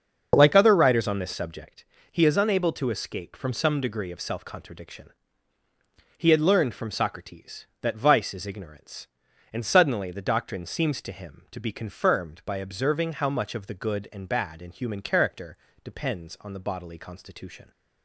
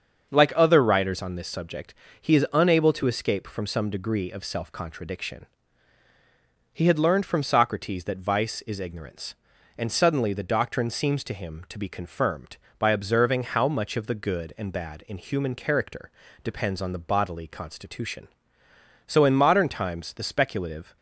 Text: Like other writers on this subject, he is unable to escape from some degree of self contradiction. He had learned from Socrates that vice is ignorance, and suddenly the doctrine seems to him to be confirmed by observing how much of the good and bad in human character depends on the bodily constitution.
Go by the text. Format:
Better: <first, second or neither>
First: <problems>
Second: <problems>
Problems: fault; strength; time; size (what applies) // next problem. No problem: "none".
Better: first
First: starts louder than the rest; until 1.3 s; 6.5 dB // pauses between "character" and "depends"; slight; at 15.5 s; 0.28 s long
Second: starts louder than the rest; until 1.3 s; 7 dB // pauses between "character" and "depends"; slight; at 16.1 s; 0.32 s long // goes on to say "So in modern times the speculative"; strong; from 19.0 s on; 1.9 s long